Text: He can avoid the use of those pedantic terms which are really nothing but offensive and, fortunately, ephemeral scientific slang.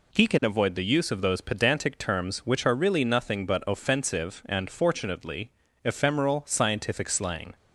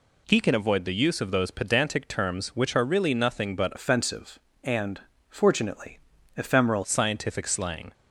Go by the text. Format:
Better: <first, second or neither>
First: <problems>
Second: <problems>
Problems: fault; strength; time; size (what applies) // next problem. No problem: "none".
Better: first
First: none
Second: changes voice from "offensive" to "ephemeral"; from 3.7 to 6.8 s; 3.1 s long